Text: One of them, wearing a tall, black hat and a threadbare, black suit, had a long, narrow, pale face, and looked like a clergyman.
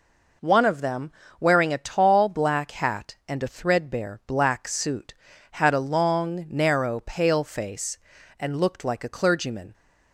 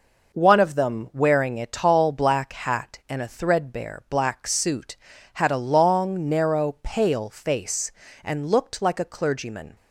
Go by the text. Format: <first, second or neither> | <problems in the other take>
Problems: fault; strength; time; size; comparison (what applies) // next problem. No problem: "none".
neither | none